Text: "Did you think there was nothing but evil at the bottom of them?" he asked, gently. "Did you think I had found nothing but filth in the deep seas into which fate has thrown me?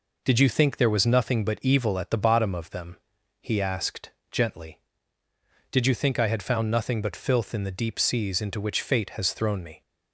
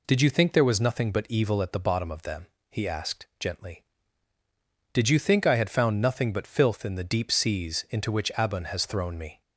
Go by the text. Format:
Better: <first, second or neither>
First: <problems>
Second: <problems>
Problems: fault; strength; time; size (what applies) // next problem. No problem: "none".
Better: first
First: none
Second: says "abun" for "fate"; at 8.3 s